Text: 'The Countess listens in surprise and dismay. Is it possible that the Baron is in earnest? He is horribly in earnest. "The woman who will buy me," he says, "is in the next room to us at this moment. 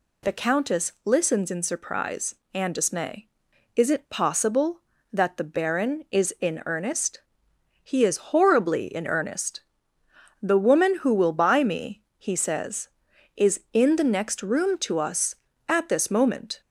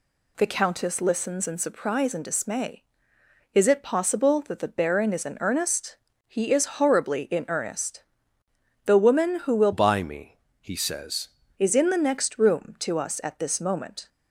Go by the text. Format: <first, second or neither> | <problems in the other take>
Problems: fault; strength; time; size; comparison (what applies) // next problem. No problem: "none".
first | changes voice from "buy" to "says"; from 9.7 to 11.2 s; 1.5 s long